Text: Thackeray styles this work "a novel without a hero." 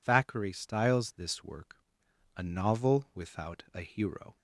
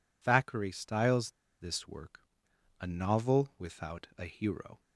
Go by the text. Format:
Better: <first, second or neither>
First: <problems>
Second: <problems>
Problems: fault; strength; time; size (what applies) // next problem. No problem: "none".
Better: first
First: pauses between "work" and "a"; noticeable; at 1.7 s; 0.62 s long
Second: pauses between "styles" and "this"; slight; at 1.3 s; 0.28 s long // pauses between "work" and "a"; noticeable; at 2.1 s; 0.62 s long